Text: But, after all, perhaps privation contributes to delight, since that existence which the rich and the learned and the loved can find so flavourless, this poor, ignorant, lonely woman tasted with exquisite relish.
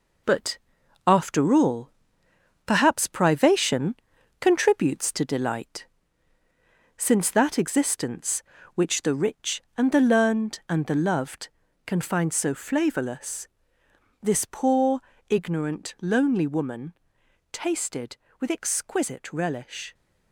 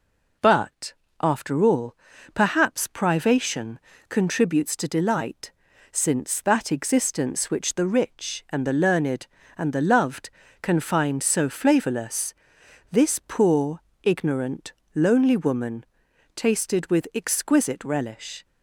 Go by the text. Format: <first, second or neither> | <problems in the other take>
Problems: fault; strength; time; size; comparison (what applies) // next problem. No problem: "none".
second | gets quieter; noticeable; throughout; 6 dB // pauses between "privation" and "contributes"; at 3.9 s; 0.44 s long; slight in the second // pauses between "woman" and "tasted"; noticeable; at 16.9 s; 0.58 s long; noticeable in the second